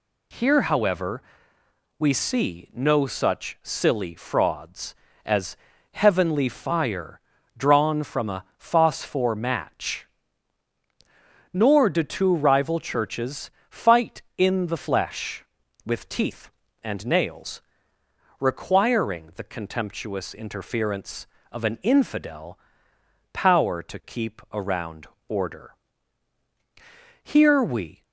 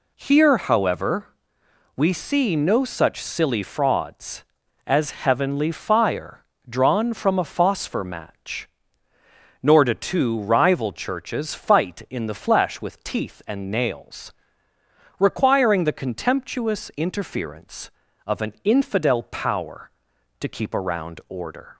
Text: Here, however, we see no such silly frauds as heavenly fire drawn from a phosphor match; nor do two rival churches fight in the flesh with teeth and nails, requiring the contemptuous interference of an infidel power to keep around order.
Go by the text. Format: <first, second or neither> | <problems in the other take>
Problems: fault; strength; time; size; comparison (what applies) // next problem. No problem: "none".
second | pauses between "as" and "heavenly"; slight; at 5.5 s; 0.34 s long // pauses between "fire" and "drawn"; at 7.1 s; 0.38 s long; slight in the second // pauses between "churches" and "fight"; slight; at 13.4 s; 0.18 s long // pauses between "infidel" and "power"; noticeable; at 22.5 s; 0.76 s long // pauses between "around" and "order"; slight; at 25.0 s; 0.22 s long // goes on to say "Here we"; noticeable; from 27.2 s on; 0.80 s long